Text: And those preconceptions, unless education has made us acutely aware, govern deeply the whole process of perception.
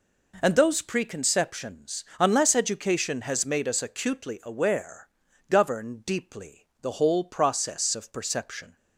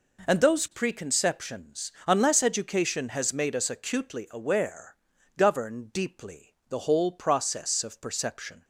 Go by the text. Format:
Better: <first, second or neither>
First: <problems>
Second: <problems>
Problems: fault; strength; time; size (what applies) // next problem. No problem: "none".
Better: neither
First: none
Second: none